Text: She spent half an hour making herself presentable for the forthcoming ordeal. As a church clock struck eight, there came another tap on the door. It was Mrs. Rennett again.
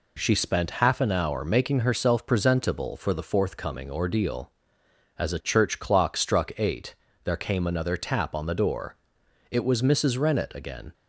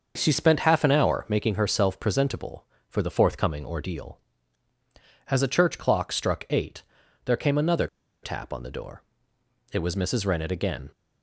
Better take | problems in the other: first | starts louder than the rest; until 1.1 s; 6 dB // pauses between "another" and "tap"; at 7.8 s; 0.36 s long

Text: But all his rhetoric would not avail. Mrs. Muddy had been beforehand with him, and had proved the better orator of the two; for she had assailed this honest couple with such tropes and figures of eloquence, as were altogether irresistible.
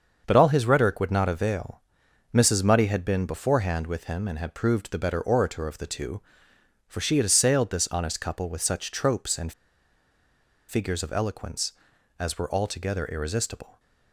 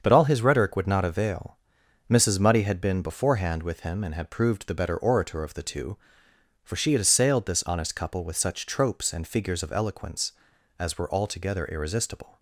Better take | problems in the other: second | starts louder than the rest; until 1.2 s; 7 dB; also in the second // pauses between "and" and "figures"; at 9.5 s; 1.1 s long

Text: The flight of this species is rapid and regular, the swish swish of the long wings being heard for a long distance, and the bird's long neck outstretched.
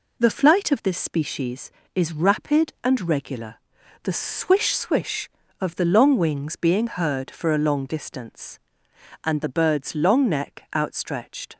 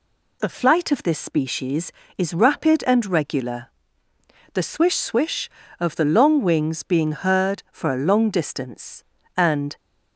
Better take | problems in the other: first | stops before "the bird's long neck outstretched"; at 9.7 s

